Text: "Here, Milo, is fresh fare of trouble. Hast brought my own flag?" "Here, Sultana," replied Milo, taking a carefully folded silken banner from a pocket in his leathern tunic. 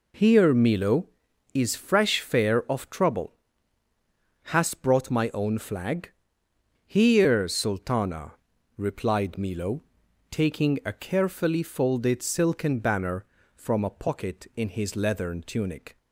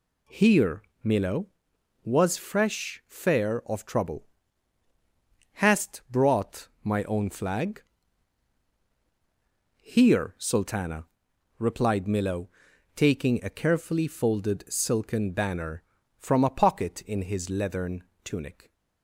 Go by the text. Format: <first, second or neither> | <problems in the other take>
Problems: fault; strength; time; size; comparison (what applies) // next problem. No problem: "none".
first | says "was" for "is"; at 2.0 s // pauses between "brought" and "my"; slight; at 6.6 s; 0.16 s long // pauses between "leathern" and "tunic"; slight; at 18.0 s; 0.22 s long